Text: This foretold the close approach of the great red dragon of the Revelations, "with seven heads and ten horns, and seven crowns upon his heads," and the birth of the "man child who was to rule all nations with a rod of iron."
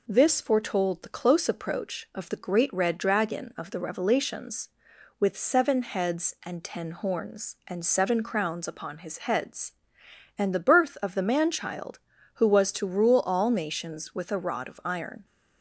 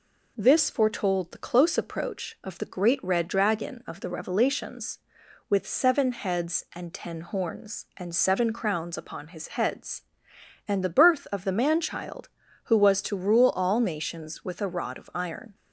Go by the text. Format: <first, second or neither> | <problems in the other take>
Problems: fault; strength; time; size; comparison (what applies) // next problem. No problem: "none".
neither | none